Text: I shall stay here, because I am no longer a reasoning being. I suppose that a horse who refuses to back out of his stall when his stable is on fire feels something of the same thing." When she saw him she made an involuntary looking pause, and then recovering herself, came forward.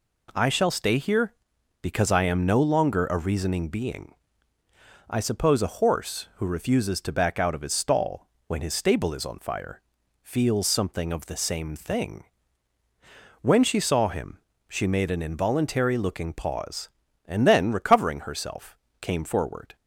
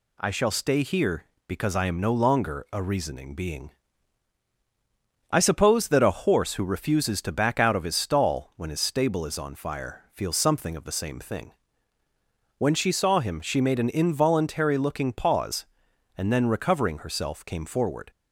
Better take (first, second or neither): second